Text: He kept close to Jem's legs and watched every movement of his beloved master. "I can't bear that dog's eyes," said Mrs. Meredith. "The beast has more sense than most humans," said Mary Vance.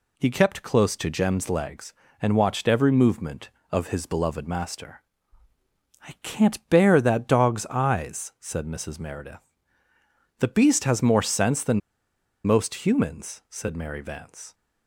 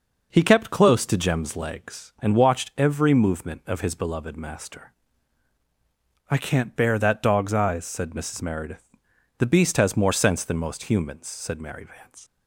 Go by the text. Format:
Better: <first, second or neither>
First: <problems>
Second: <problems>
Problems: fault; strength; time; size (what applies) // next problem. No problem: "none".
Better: second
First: pauses between "than" and "most"; noticeable; at 11.8 s; 0.65 s long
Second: none